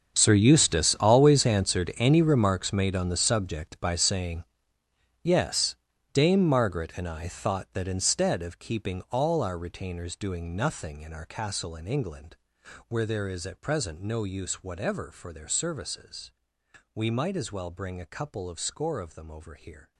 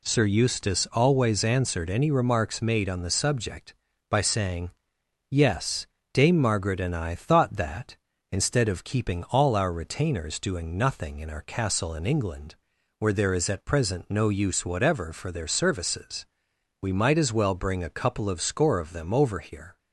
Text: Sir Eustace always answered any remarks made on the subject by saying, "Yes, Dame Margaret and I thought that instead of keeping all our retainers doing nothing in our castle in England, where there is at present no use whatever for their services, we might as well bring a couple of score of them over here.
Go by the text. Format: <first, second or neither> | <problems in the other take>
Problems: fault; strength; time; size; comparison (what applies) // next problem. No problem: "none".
second | gets quieter; strong; throughout; 18 dB